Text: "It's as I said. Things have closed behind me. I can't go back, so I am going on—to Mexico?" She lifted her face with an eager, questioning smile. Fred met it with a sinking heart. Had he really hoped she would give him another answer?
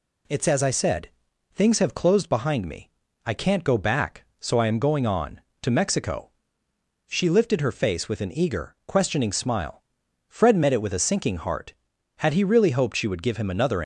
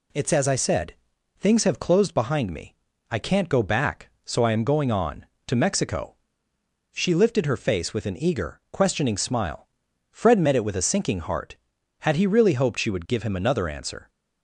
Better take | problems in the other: second | stops before "answer"; at 13.8 s

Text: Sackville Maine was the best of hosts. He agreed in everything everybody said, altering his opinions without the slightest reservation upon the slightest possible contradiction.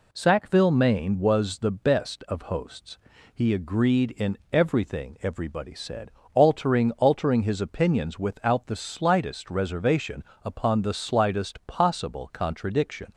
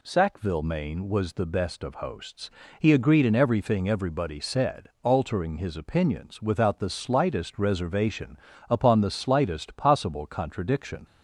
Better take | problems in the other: second | says "altering" twice; at 6.9 s // pauses between "reservation" and "upon"; slight; at 10.2 s; 0.18 s long; slight in the second

